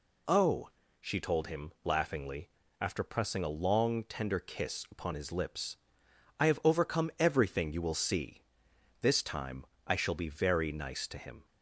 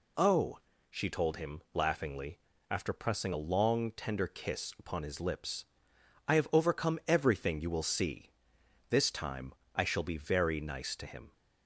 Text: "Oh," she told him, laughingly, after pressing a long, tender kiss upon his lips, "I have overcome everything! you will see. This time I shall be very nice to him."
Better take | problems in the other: neither | pauses between "time" and "I"; slight; the same in both

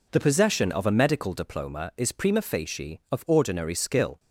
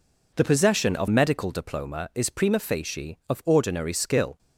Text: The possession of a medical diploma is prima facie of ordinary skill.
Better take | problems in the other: first | skips "a"; at 1.0 s

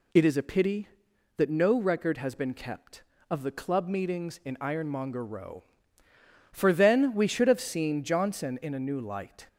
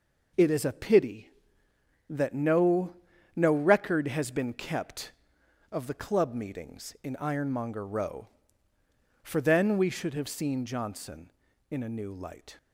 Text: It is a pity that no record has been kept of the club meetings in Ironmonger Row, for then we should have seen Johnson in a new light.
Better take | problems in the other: first | says "no" twice; at 3.3 s

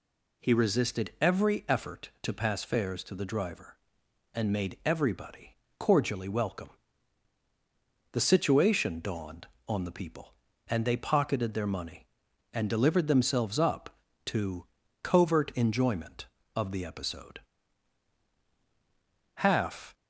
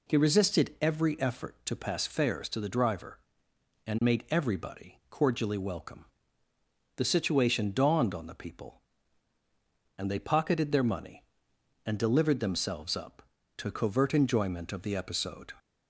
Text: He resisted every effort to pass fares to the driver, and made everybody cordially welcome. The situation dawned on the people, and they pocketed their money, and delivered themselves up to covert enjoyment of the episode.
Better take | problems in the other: second | pauses between "everybody" and "cordially"; slight; at 5.5 s; 0.24 s long // pauses between "to" and "covert"; at 14.6 s; 0.38 s long // goes on to say "Half"; from 19.3 s on; 0.58 s long

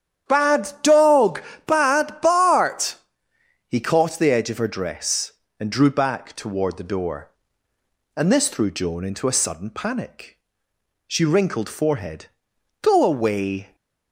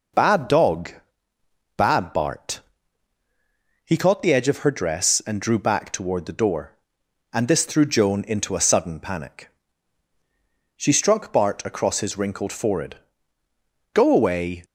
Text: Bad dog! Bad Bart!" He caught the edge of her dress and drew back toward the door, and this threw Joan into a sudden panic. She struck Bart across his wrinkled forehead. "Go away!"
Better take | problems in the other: second | starts louder than the rest; strong; until 1.3 s; 9.5 dB // skips "struck Bart across his"; at 11.2 s

